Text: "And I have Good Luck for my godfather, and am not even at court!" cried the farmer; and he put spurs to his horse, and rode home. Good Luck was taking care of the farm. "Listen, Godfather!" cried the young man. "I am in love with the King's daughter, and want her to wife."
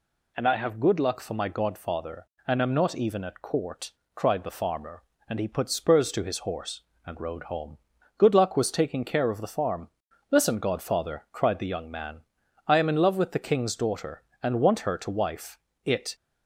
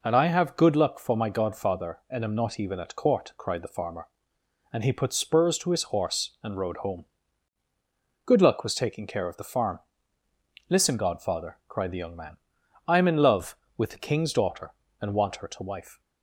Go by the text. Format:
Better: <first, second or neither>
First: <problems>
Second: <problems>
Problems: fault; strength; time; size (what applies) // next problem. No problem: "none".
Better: second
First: goes on to say "It"; slight; from 15.8 s on; 0.32 s long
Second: none